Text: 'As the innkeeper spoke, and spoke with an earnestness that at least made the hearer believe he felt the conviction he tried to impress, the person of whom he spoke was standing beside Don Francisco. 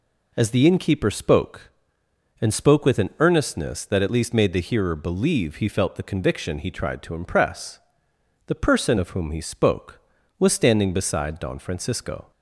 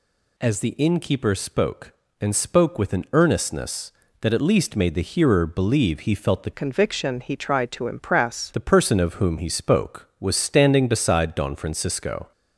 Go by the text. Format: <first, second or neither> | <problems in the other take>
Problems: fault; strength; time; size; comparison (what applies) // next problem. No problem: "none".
first | changes voice from "conviction" to "impress"; from 6.5 to 8.5 s; 2.0 s long